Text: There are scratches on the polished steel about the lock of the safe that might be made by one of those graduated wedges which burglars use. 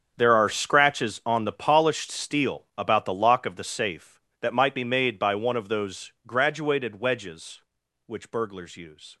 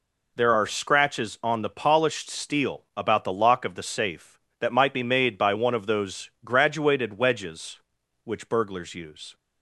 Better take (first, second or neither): second